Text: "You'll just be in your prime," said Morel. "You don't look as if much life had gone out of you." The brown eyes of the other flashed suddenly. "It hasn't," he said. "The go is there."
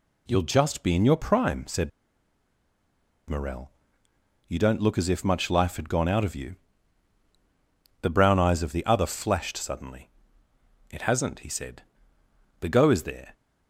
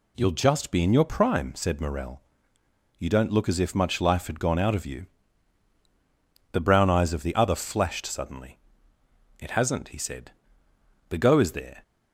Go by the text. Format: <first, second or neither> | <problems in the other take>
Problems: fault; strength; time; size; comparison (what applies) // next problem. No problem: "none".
second | pauses between "said" and "Morel"; strong; at 1.8 s; 1.3 s long